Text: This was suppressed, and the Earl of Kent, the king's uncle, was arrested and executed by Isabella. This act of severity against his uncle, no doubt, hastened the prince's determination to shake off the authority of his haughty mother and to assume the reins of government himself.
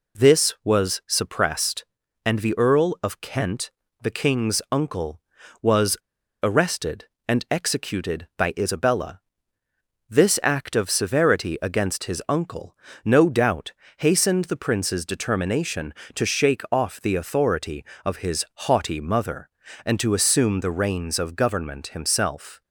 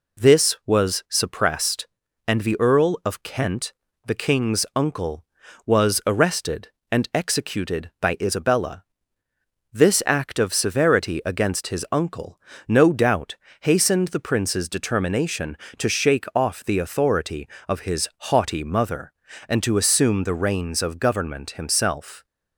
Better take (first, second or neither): second